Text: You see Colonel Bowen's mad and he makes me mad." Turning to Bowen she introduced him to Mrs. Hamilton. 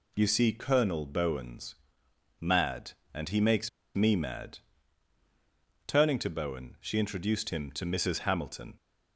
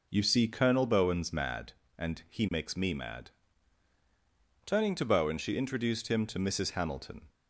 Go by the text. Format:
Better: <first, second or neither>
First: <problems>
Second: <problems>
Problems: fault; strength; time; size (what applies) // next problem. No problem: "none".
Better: second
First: pauses between "Bowen's" and "mad"; noticeable; at 1.7 s; 0.64 s long // pauses between "makes" and "me"; slight; at 3.6 s; 0.26 s long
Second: none